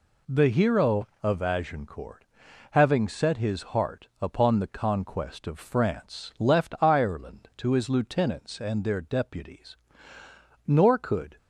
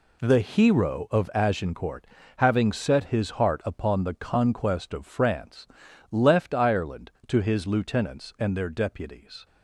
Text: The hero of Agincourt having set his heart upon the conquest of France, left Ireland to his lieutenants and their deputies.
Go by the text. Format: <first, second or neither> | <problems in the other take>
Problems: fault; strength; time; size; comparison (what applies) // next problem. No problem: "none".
second | pauses between "Agincourt" and "having"; noticeable; at 2.2 s; 0.46 s long; slight in the second // goes on to say "Nor could"; noticeable; from 10.6 s on; 0.70 s long